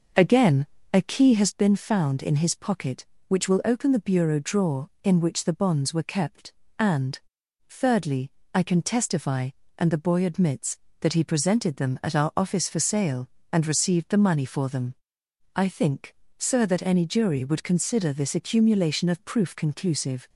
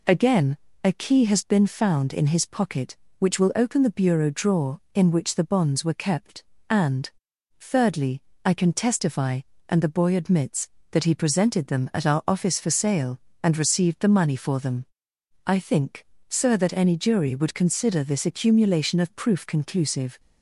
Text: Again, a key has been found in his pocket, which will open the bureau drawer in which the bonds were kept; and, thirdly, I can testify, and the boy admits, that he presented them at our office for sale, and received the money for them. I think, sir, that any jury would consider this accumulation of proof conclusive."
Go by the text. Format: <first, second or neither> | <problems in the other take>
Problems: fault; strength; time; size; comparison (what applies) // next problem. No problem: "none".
second | starts louder than the rest; noticeable; until 1.5 s; 6 dB